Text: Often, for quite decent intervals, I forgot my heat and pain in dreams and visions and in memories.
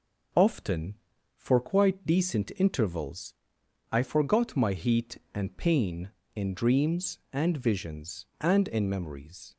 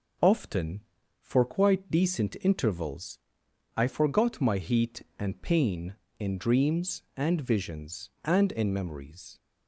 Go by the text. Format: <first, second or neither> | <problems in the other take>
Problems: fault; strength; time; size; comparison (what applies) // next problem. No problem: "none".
neither | none